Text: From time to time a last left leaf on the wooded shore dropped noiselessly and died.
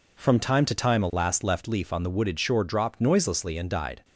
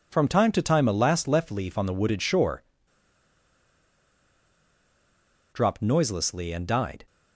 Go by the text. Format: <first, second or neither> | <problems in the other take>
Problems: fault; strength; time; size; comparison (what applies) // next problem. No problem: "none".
first | pauses between "shore" and "dropped"; strong; at 2.6 s; 2.8 s long